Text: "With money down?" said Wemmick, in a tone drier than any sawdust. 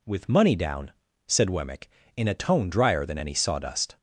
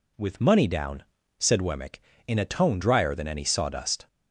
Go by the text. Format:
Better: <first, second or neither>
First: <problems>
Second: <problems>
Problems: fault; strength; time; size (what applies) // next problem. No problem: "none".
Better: neither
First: none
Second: none